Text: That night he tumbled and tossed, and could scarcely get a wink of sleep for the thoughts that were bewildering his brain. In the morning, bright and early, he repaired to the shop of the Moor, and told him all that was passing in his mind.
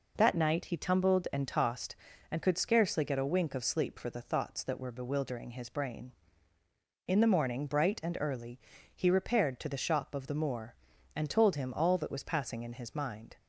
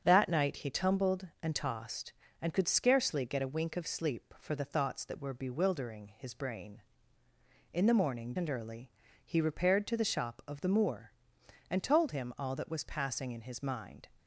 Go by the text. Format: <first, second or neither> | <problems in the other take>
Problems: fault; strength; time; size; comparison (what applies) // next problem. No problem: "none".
first | starts louder than the rest; strong; until 1.0 s; 7 dB // skips "bright"; at 8.3 s